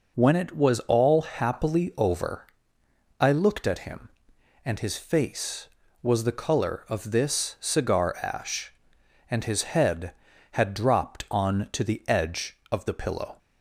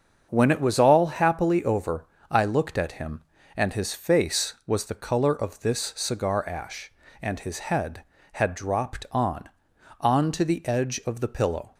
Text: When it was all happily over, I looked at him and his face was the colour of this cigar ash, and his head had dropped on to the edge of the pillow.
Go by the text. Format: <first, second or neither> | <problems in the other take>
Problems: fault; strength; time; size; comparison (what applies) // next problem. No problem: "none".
first | starts louder than the rest; until 1.3 s; 7 dB // says "on" twice; at 9.9 s